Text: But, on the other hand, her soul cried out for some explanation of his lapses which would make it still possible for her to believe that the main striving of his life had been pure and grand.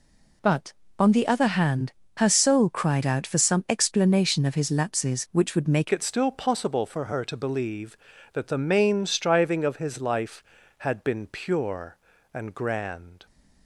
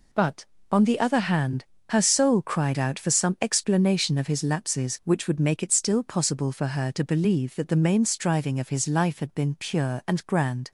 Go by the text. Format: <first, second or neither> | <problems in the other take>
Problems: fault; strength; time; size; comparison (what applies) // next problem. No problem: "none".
second | changes voice at "it"; from 5.9 s on; 7.3 s long